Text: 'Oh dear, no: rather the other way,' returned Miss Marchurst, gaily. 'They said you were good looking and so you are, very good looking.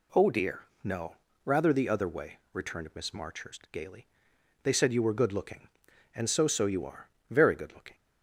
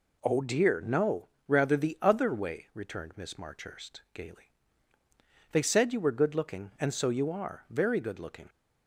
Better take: second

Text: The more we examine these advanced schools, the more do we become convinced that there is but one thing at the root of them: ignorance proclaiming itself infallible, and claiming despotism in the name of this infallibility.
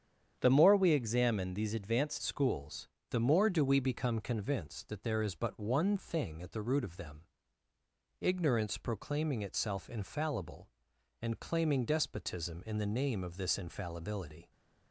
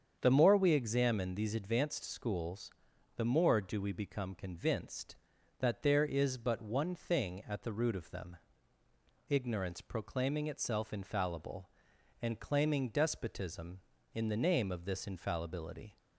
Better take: second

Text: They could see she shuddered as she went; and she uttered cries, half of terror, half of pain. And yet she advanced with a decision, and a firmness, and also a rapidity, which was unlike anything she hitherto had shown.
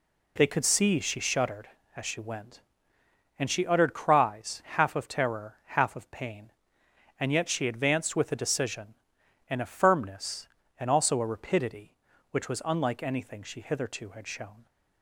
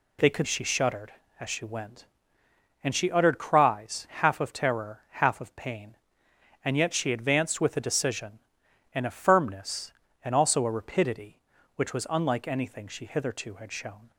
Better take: first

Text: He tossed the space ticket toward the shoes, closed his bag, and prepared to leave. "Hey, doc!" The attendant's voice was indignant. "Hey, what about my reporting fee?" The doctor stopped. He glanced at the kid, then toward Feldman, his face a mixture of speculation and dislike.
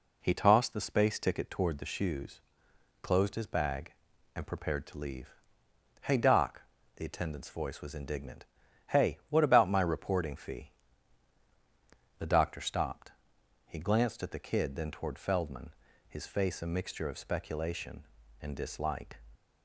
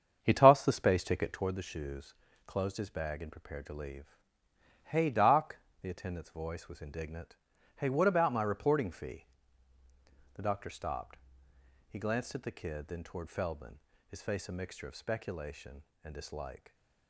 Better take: first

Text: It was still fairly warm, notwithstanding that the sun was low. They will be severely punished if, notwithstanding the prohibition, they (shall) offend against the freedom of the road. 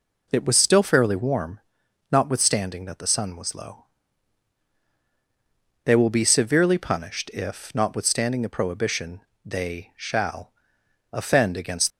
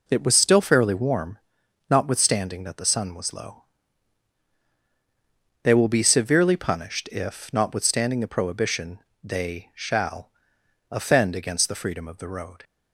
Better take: second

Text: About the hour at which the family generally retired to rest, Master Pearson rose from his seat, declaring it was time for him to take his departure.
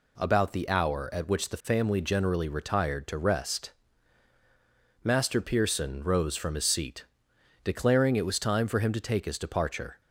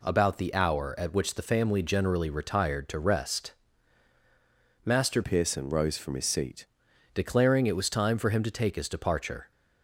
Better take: first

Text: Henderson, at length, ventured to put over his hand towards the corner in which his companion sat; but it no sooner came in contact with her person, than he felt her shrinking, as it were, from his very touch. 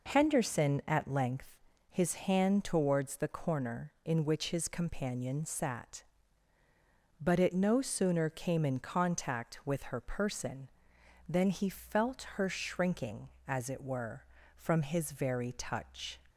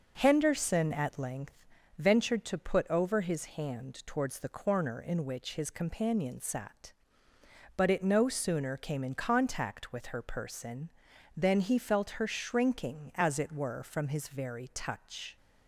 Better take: second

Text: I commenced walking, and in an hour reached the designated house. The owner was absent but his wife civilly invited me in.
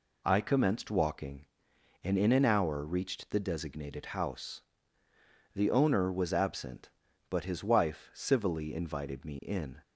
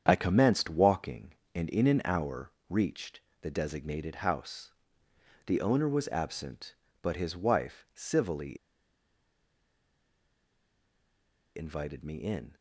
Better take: first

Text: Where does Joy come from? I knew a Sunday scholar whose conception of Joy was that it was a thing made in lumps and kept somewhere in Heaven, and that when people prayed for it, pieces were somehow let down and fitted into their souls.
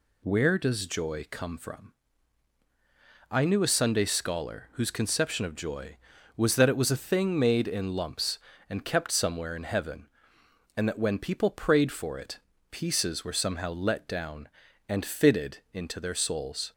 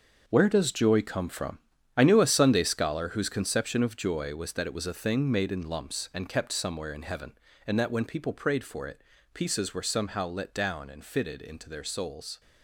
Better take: first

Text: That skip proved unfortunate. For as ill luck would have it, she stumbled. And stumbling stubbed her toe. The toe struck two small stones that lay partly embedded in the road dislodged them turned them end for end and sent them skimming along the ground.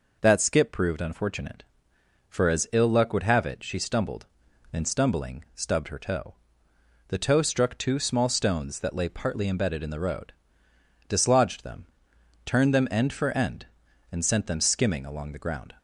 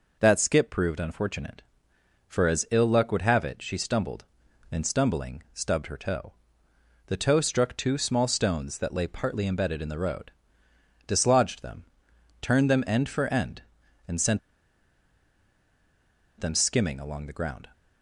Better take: first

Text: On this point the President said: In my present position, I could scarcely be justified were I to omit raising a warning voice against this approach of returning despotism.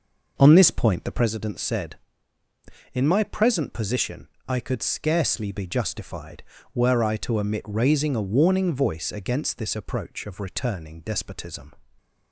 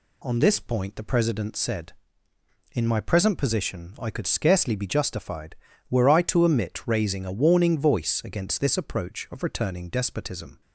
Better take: second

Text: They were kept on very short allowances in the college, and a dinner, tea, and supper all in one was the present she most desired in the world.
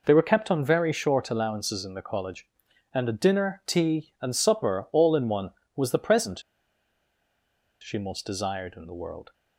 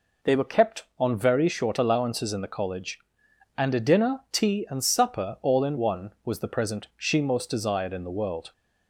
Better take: second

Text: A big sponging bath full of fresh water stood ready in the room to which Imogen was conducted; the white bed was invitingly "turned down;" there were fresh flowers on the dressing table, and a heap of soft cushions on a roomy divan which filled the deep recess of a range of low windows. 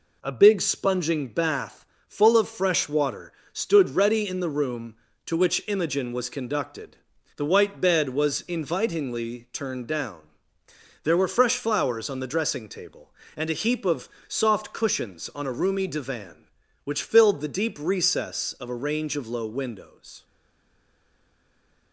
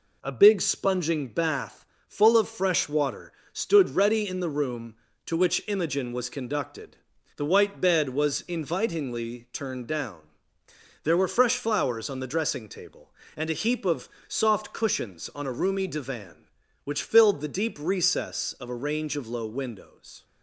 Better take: second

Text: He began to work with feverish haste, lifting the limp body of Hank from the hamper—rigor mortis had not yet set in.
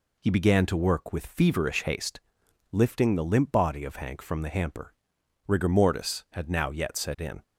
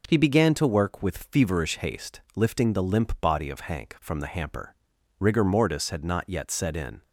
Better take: second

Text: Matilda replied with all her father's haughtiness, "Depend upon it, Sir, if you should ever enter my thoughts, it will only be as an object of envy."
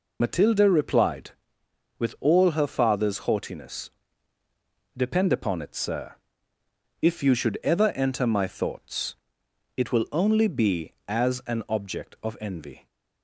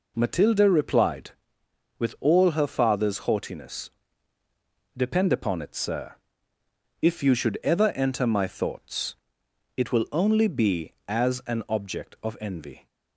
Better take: second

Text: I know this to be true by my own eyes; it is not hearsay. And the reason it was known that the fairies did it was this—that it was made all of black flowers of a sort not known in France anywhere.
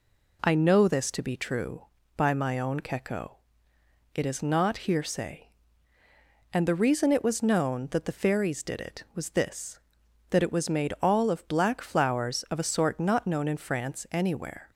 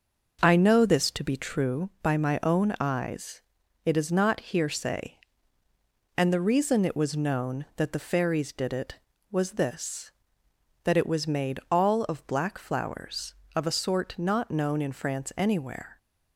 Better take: second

